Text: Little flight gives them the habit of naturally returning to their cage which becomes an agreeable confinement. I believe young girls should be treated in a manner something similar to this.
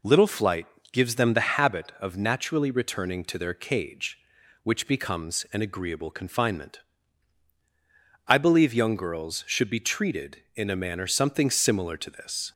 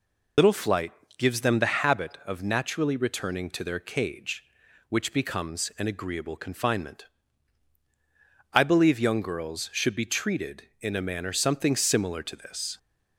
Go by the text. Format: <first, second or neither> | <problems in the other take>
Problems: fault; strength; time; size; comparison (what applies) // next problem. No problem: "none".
first | loses the start of "Little"; at 0.3 s; 80 ms // pauses between "flight" and "gives"; slight; at 0.9 s; 0.24 s long; slight in the first